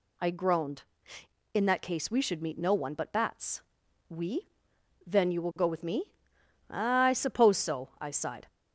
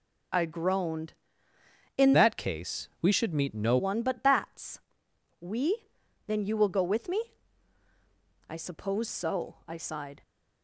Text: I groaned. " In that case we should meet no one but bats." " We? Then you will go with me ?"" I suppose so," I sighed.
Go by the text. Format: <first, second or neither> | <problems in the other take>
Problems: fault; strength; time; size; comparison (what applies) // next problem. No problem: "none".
first | changes voice from "that" to "no"; from 2.1 to 3.7 s; 1.6 s long